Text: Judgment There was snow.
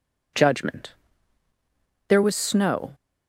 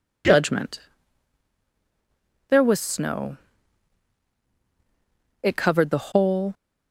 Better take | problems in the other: first | pauses between "Judgment" and "There"; strong; at 0.7 s; 1.7 s long; also in the first // goes on to say "It covered the whole"; noticeable; from 5.4 s on; 1.0 s long

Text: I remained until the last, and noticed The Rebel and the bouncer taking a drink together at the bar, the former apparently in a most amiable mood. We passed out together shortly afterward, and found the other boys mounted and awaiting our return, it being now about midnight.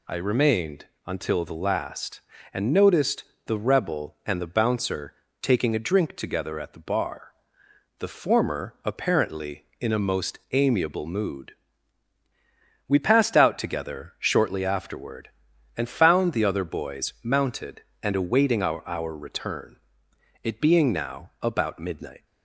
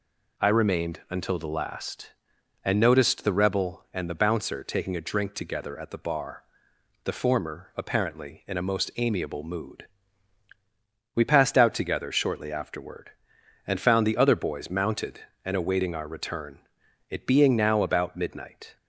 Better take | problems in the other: second | pauses between "remained" and "until"; slight; at 0.8 s; 0.22 s long // pauses between "noticed" and "The"; slight; at 3.2 s; 0.24 s long // pauses between "bouncer" and "taking"; slight; at 5.1 s; 0.28 s long // says "our" twice; at 18.8 s

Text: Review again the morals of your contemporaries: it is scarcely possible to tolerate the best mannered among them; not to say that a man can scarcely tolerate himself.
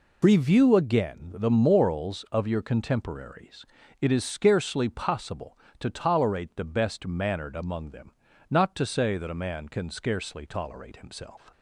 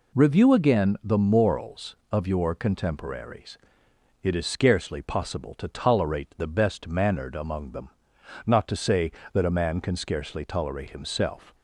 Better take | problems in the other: neither | none

